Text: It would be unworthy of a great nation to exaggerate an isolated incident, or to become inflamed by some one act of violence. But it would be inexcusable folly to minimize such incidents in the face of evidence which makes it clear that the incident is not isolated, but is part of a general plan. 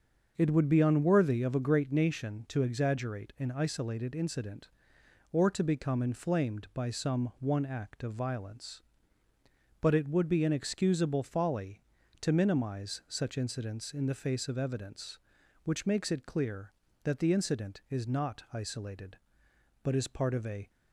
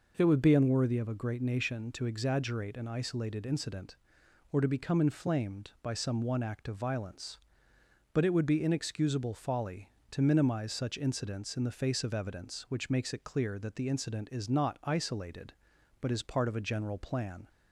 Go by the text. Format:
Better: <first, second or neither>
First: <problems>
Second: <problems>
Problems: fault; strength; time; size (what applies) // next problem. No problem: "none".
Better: second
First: starts louder than the rest; until 1.3 s; 6.5 dB // stops before "general plan"; at 20.6 s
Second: none